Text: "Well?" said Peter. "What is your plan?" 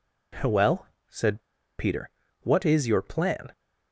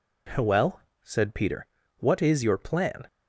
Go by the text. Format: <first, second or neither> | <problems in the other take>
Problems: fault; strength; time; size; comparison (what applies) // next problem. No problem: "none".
second | pauses between "said" and "Peter"; at 1.3 s; 0.38 s long